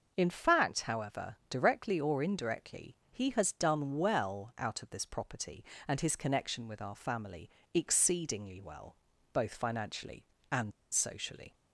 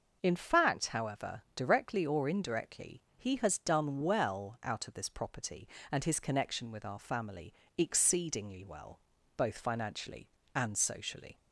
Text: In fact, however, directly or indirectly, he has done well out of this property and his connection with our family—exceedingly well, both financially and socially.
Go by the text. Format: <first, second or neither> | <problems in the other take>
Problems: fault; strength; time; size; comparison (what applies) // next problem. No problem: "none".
second | starts louder than the rest; until 1.1 s; 6 dB; noticeable in the second // pauses between "and" and "socially"; slight; at 10.7 s; 0.20 s long